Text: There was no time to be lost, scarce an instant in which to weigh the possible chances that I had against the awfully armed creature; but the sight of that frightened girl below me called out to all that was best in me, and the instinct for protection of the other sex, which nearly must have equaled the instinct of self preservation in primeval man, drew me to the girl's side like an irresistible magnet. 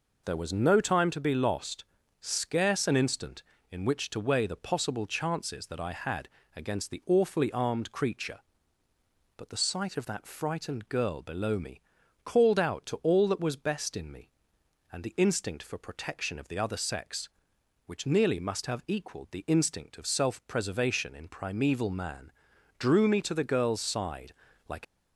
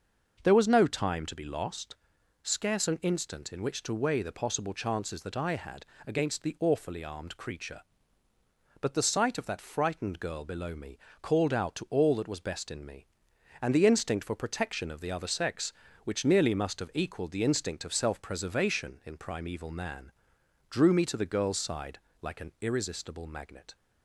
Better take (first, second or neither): second